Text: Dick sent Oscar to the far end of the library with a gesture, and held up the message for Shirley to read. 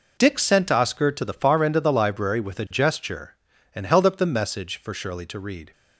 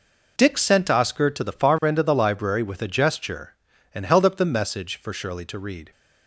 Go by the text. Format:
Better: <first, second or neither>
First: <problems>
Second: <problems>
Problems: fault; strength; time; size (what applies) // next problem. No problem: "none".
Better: neither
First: none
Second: none